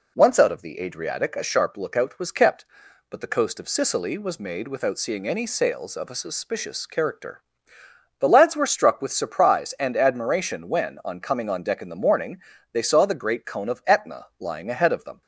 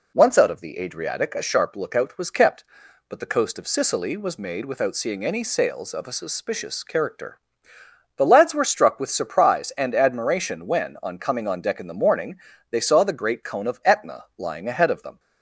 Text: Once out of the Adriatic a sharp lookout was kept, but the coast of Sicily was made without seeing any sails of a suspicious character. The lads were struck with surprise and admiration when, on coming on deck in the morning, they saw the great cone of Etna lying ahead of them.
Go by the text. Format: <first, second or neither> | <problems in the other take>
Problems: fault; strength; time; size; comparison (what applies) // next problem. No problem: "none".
neither | none